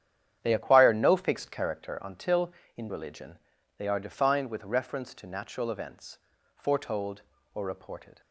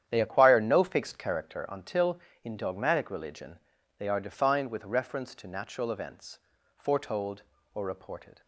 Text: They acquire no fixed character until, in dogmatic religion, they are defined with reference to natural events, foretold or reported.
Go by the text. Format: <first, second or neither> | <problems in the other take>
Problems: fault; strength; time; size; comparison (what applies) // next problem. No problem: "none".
second | starts louder than the rest; strong; until 1.4 s; 9.5 dB; strong in the second // skips "dogmatic"; at 2.8 s